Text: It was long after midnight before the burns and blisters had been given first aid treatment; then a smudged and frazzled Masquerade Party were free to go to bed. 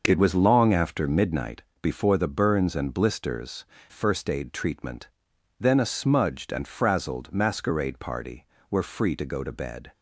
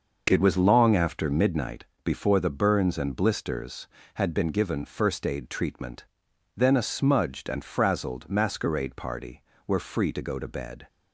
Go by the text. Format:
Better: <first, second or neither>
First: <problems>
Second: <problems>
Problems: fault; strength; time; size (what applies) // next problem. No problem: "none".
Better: second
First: starts louder than the rest; noticeable; until 1.0 s; 6 dB // pauses between "midnight" and "before"; slight; at 1.6 s; 0.20 s long // skips "had been given"; at 3.7 s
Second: pauses between "midnight" and "before"; slight; at 1.8 s; 0.20 s long